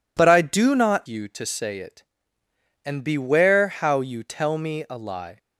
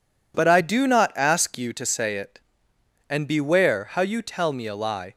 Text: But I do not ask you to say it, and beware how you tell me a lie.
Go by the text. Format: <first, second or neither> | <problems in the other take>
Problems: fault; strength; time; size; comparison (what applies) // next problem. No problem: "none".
second | skips "ask"; at 1.0 s